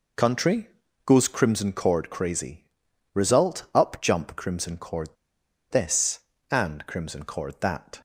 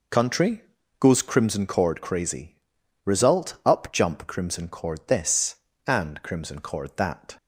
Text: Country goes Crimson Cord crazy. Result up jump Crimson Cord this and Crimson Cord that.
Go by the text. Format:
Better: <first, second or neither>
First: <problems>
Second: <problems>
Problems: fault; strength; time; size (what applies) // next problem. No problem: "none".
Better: second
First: pauses between "Country" and "goes"; at 0.6 s; 0.38 s long // pauses between "Cord" and "this"; noticeable; at 5.0 s; 0.63 s long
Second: pauses between "Country" and "goes"; at 0.6 s; 0.38 s long